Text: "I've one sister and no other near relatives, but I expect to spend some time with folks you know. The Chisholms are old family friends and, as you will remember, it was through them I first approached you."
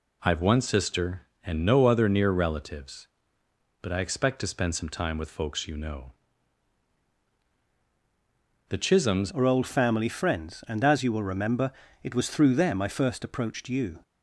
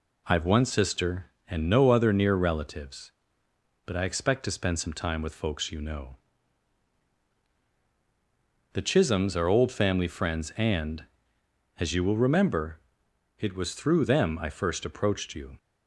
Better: second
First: changes voice at "are"; from 9.3 s on; 4.7 s long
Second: none

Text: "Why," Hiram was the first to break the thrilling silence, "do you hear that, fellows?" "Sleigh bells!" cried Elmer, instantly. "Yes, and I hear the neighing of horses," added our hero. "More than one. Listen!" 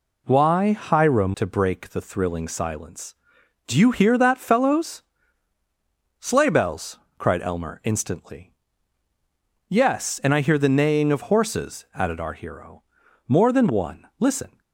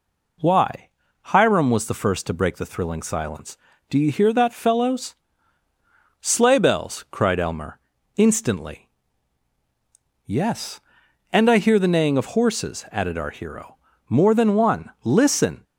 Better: second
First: skips "was the first"; at 1.3 s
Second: none

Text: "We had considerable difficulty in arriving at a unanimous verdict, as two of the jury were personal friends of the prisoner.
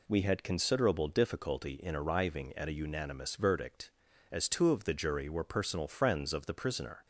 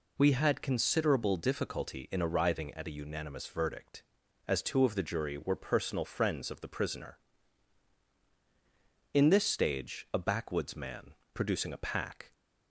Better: first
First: none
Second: goes on to say "In this stage a backwoods man producing a pack"; strong; from 9.1 s on; 3.2 s long

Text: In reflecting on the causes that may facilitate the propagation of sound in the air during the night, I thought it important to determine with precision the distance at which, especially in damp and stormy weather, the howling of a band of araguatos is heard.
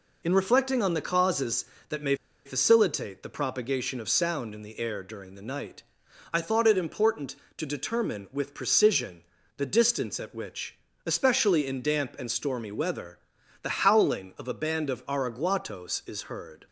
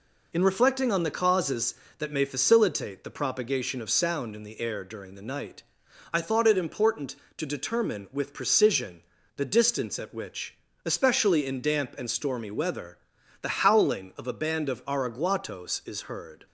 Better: second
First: pauses between "may" and "facilitate"; slight; at 2.1 s; 0.31 s long // pauses between "precision" and "the"; slight; at 9.2 s; 0.36 s long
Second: pauses between "precision" and "the"; slight; at 9.0 s; 0.36 s long

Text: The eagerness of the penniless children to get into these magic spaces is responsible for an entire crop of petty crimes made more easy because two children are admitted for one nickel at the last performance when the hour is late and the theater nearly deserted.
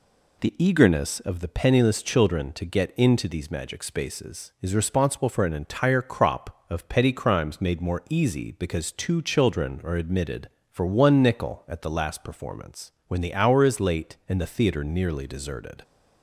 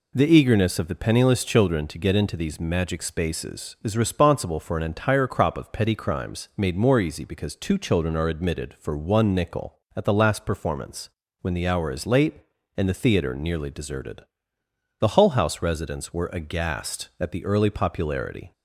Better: first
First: pauses between "performance" and "when"; slight; at 12.9 s; 0.16 s long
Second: pauses between "performance" and "when"; slight; at 11.0 s; 0.32 s long // goes on to say "The Hull House residents were aghast at the early popularity"; strong; from 15.0 s on; 3.5 s long

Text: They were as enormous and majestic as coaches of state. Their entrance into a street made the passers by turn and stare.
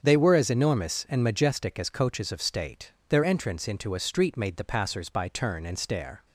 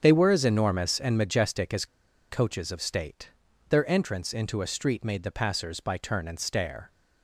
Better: first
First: starts louder than the rest; until 1.0 s; 7 dB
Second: starts louder than the rest; strong; until 1.0 s; 7.5 dB // pauses between "as" and "coaches"; at 1.8 s; 0.45 s long

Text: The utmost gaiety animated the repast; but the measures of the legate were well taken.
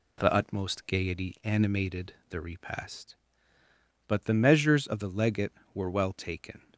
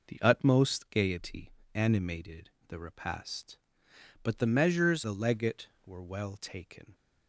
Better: first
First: pauses between "animated" and "the"; slight; at 2.1 s; 0.18 s long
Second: pauses between "gaiety" and "animated"; slight; at 1.5 s; 0.22 s long // pauses between "animated" and "the"; slight; at 2.4 s; 0.18 s long // skips "of"; at 5.0 s

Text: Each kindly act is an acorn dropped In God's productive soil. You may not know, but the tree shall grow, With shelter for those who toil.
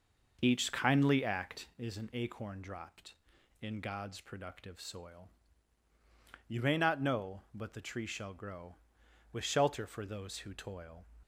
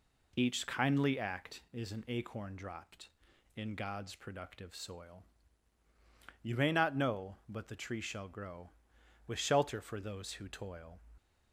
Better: second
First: starts louder than the rest; noticeable; until 1.9 s; 6 dB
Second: none

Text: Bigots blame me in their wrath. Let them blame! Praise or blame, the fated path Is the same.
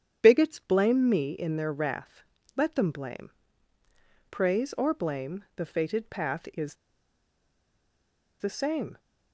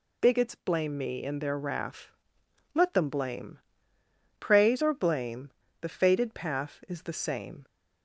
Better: second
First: starts louder than the rest; strong; until 1.2 s; 9 dB // pauses between "Is" and "the"; strong; at 6.7 s; 1.6 s long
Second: none

